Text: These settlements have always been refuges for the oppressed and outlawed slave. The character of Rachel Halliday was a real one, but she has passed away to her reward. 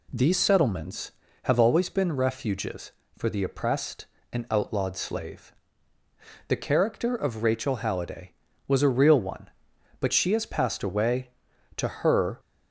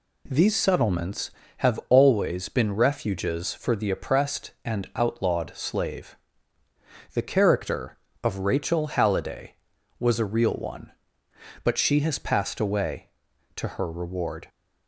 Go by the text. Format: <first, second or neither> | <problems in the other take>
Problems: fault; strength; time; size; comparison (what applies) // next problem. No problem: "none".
second | stops before "reward"; at 12.3 s